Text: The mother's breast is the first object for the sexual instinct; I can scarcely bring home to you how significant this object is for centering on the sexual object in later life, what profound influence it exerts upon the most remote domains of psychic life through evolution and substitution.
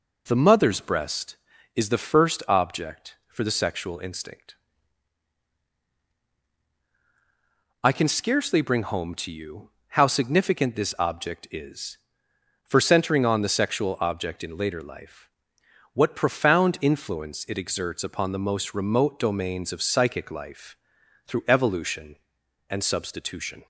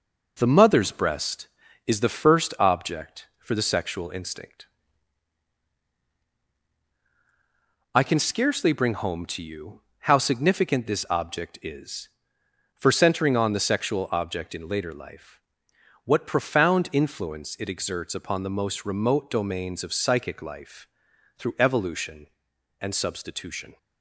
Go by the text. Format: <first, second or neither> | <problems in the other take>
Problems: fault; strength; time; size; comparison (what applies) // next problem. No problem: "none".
first | gets quieter; noticeable; throughout; 4.5 dB // pauses between "you" and "how"; slight; at 9.8 s; 0.20 s long; slight in the first // pauses between "life" and "through"; noticeable; at 20.8 s; 0.50 s long; noticeable in the first